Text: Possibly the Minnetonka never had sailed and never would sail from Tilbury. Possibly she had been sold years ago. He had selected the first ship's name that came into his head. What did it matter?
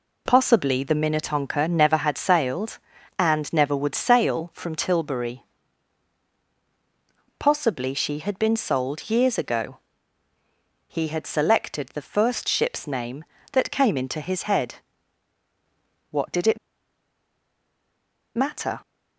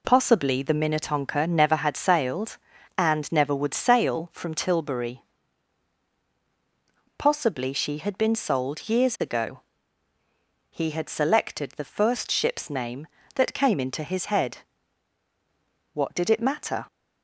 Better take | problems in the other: second | pauses between "it" and "matter"; strong; at 16.5 s; 1.7 s long

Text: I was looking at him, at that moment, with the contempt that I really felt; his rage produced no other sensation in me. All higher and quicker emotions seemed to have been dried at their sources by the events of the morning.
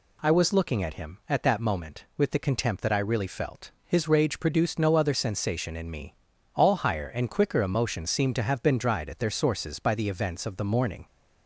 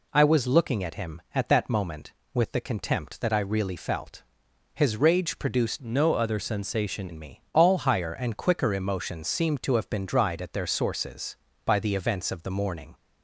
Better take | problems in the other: first | changes voice from "no" to "sensation"; from 5.7 to 7.1 s; 1.4 s long

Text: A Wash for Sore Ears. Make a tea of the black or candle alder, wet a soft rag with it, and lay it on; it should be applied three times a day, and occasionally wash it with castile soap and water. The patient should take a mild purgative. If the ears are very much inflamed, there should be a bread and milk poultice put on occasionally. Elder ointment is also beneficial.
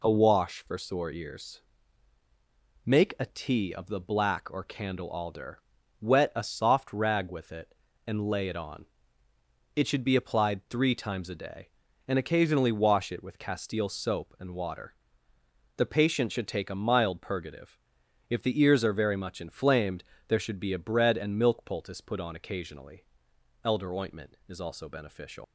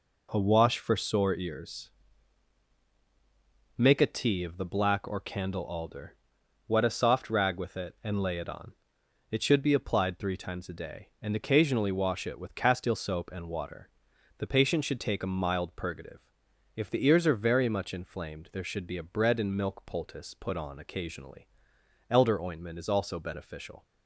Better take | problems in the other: second | leaves "beneficial" unfinished; at 25.4 s; 210 ms

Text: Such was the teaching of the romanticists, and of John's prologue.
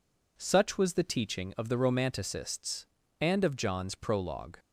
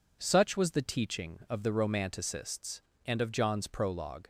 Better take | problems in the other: neither | none

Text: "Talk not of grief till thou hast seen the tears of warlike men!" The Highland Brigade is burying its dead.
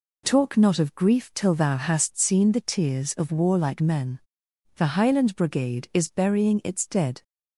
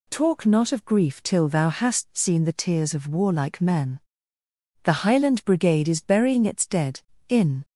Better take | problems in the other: first | goes on to say "In"; slight; from 7.2 s on; 0.36 s long

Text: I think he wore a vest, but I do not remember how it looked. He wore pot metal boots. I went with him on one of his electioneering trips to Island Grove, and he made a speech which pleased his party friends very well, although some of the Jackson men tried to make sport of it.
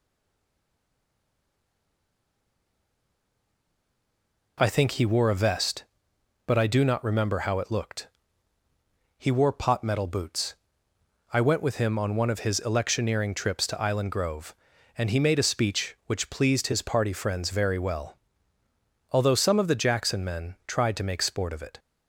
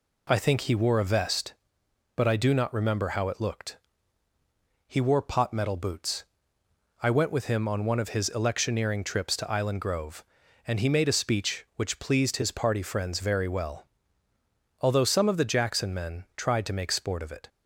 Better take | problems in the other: second | stays silent before the first word; strong; until 4.5 s; 4.5 s long

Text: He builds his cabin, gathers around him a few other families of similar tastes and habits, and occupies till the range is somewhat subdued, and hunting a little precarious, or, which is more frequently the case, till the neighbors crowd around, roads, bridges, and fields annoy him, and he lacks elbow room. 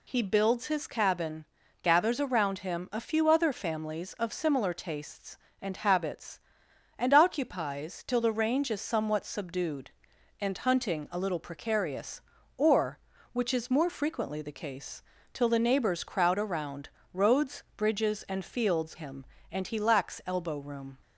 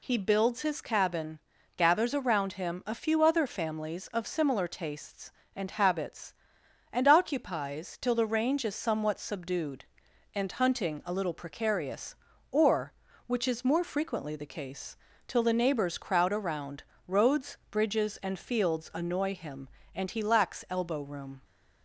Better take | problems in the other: second | skips "annoy"; at 18.9 s

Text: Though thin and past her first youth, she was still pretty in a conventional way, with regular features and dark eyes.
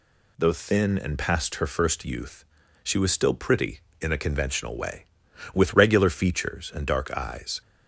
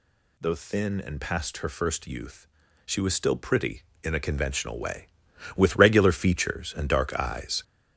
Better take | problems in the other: first | gets louder; strong; throughout; 7.5 dB

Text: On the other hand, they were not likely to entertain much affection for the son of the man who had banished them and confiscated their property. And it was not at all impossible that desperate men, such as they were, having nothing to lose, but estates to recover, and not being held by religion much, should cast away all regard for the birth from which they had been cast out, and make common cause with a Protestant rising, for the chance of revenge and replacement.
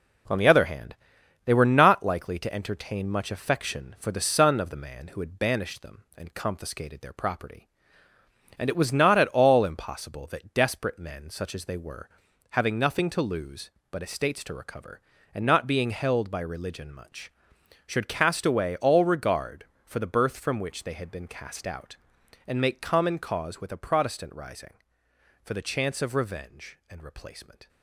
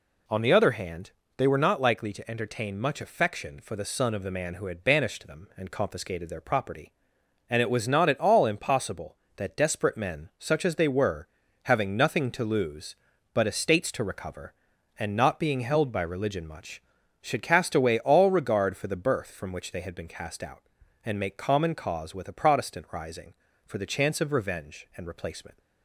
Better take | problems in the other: second | gets quieter; noticeable; throughout; 5 dB

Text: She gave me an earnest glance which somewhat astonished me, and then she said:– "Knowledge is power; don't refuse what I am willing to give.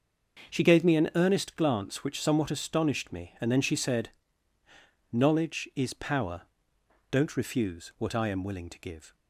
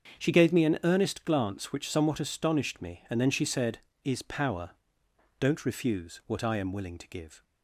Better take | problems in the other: first | starts louder than the rest; strong; until 1.2 s; 7 dB; noticeable in the first // skips "Knowledge"; at 3.9 s

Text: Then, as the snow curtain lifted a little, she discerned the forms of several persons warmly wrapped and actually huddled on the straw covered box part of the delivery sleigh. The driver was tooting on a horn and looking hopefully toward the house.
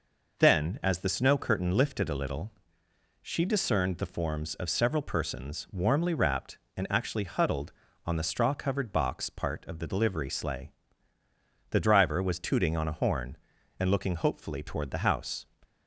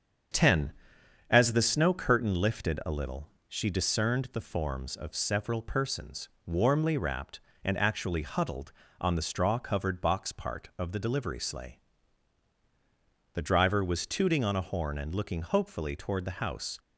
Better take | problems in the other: first | starts louder than the rest; strong; until 1.8 s; 7.5 dB // says "Ten" for "Then"; at 0.3 s // pauses between "persons" and "warmly"; slight; at 6.2 s; 0.18 s long

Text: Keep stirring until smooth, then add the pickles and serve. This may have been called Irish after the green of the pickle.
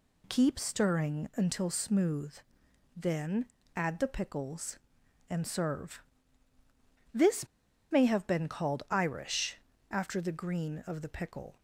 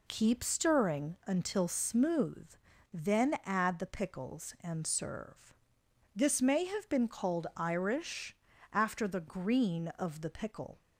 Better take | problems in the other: second | pauses between "then" and "add"; slight; at 3.4 s; 0.30 s long // pauses between "This" and "may"; at 7.4 s; 0.43 s long // pauses between "Irish" and "after"; slight; at 9.5 s; 0.34 s long; also in the second

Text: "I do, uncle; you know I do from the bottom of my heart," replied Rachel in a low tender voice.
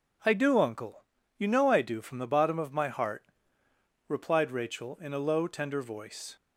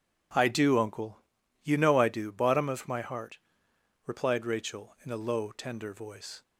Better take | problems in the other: first | skips "from the"; at 2.3 s

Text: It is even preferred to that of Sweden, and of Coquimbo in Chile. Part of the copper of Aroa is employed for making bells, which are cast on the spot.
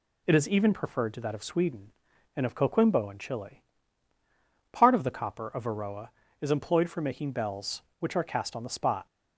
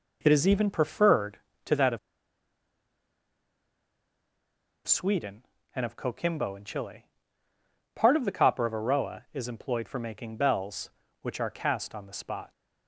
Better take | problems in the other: first | pauses between "of" and "Sweden"; strong; at 1.9 s; 2.8 s long

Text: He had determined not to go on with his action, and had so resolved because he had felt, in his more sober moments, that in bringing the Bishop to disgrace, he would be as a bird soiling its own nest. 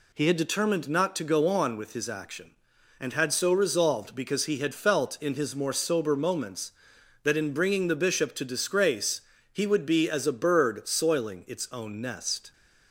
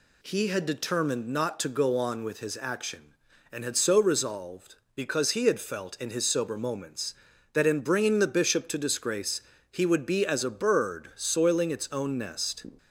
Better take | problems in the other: first | skips "more"; at 6.2 s

